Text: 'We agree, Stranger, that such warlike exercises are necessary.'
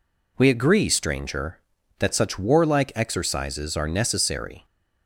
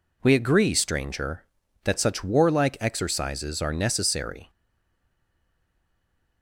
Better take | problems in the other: first | stays silent after the last word; noticeable; from 4.4 s on; 2.0 s long

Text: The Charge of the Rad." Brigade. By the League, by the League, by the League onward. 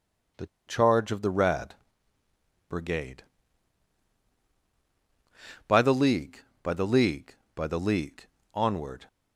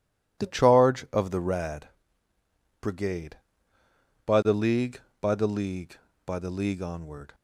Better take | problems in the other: second | pauses between "The" and "Charge"; slight; at 0.4 s; 0.20 s long // pauses between "League" and "onward"; slight; at 8.2 s; 0.26 s long

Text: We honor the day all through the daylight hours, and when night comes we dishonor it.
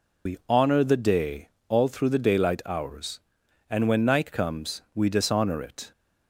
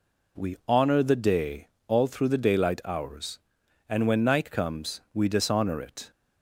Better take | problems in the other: second | loses the start of "We"; at 0.2 s; 90 ms // pauses between "day" and "all"; slight; at 1.4 s; 0.18 s long; slight in the second

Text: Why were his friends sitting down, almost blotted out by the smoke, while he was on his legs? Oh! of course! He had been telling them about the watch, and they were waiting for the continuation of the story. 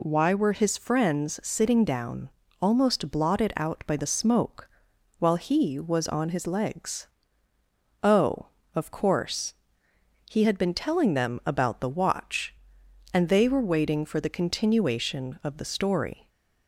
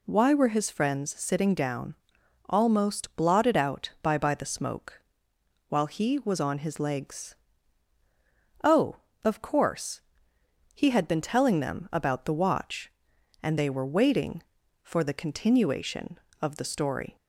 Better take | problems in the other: first | says "by" twice; at 4.1 s

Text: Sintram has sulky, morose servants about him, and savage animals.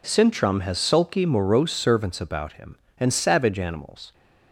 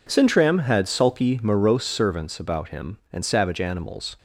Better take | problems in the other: first | says "had" for "has"; at 0.6 s

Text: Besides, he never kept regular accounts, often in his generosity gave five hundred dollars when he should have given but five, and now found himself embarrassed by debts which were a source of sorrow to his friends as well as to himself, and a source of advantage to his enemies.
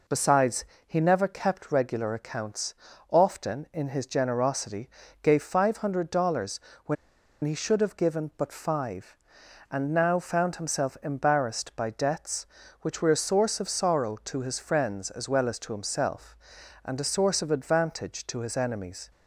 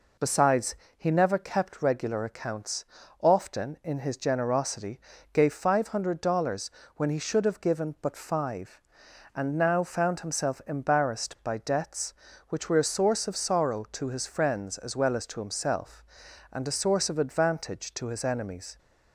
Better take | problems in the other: second | pauses between "generosity" and "gave"; slight; at 4.8 s; 0.34 s long; slight in the second // pauses between "dollars" and "when"; slight; at 6.5 s; 0.26 s long; slight in the second // pauses between "when" and "he"; noticeable; at 6.9 s; 0.48 s long

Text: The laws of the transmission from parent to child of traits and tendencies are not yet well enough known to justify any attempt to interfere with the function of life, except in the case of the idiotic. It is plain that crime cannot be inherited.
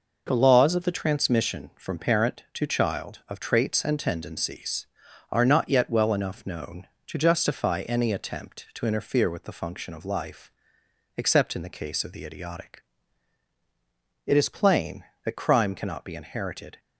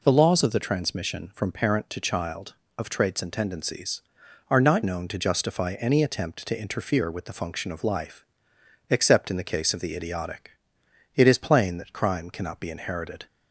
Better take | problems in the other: first | skips "yet well enough"; at 4.8 s

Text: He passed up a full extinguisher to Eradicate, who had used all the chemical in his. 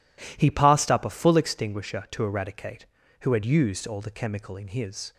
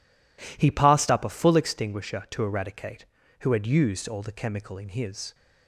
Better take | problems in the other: neither | none

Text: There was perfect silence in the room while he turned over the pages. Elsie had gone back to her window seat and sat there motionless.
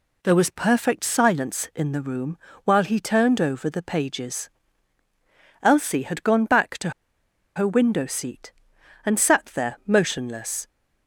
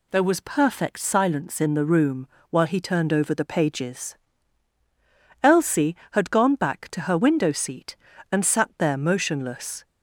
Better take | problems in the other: second | pauses between "room" and "while"; slight; at 2.3 s; 0.28 s long; slight in the second // pauses between "to" and "her"; noticeable; at 6.9 s; 0.64 s long

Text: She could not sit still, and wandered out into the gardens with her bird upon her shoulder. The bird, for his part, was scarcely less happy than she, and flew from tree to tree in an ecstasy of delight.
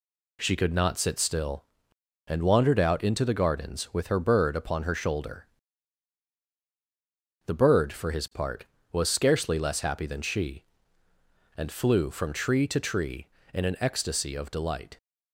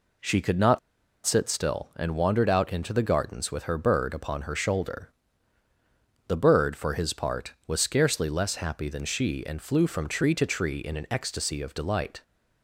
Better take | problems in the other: first | pauses between "not" and "sit"; noticeable; at 0.7 s; 0.47 s long

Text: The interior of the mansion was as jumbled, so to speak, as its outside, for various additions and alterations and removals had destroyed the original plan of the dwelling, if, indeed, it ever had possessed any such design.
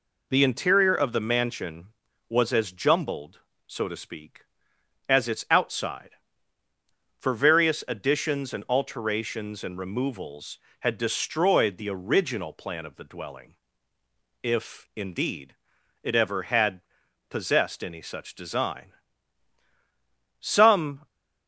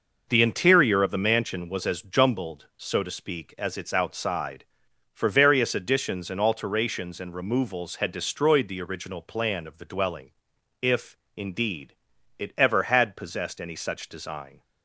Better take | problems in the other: second | pauses between "had" and "possessed"; noticeable; at 16.8 s; 0.48 s long // goes on to say "Some"; noticeable; from 20.4 s on; 0.66 s long

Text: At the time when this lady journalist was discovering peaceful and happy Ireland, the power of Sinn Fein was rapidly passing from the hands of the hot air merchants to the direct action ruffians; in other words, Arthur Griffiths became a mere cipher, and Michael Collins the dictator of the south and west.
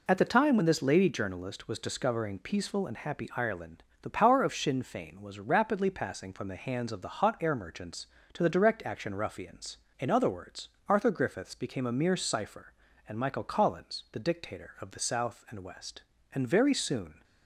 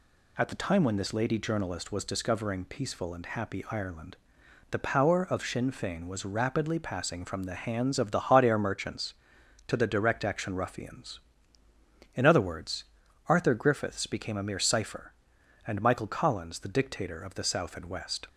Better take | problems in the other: second | goes on to say "And very soon"; noticeable; from 16.3 s on; 0.88 s long

